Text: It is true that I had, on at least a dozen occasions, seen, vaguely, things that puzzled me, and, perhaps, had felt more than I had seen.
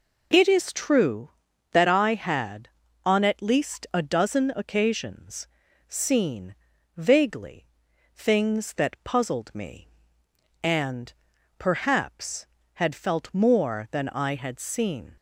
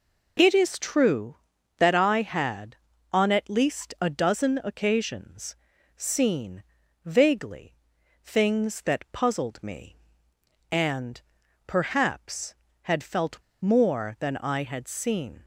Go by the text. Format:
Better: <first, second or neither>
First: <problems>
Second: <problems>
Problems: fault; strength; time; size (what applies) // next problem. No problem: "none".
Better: first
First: none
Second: pauses between "felt" and "more"; slight; at 13.3 s; 0.23 s long